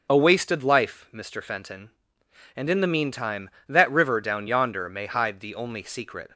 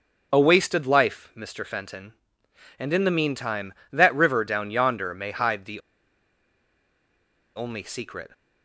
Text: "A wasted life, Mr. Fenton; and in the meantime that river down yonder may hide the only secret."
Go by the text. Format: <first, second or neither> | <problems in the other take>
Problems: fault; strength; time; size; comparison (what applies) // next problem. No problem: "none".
first | pauses between "the" and "only"; strong; at 5.8 s; 1.7 s long